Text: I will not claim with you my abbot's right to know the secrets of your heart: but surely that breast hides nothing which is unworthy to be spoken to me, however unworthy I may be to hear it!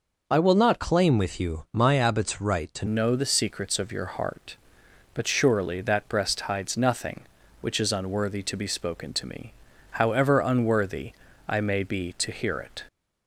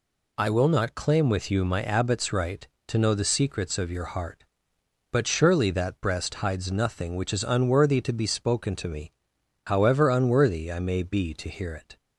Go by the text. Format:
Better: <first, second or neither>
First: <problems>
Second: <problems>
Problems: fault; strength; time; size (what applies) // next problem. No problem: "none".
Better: second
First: changes voice at "know"; from 2.8 s on; 10.0 s long // pauses between "unworthy" and "I"; slight; at 11.1 s; 0.36 s long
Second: none